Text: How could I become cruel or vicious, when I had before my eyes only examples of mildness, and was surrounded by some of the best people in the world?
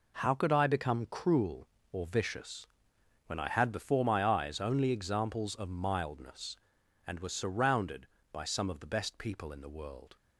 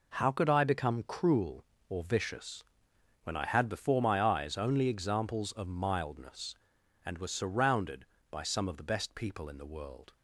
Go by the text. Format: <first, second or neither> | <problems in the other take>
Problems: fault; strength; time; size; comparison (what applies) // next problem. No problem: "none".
neither | none